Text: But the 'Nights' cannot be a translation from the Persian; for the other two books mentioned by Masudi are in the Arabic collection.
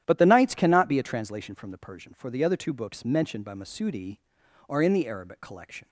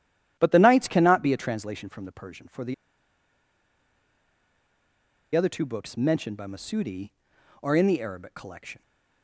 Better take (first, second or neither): first